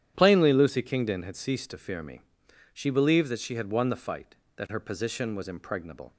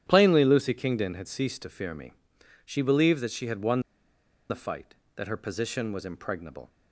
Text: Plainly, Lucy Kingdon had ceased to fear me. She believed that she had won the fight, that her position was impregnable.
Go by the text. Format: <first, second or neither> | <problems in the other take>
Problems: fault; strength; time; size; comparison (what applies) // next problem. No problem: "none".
first | starts louder than the rest; strong; until 1.0 s; 10 dB; strong in the first // pauses between "won" and "the"; noticeable; at 3.8 s; 0.68 s long